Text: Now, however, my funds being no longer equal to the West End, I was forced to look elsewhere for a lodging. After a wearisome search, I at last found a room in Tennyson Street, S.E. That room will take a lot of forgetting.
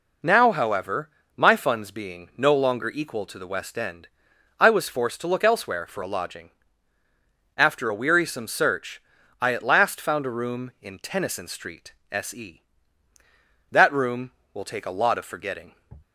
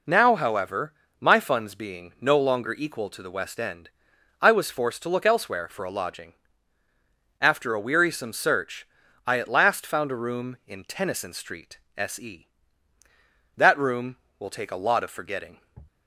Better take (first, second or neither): neither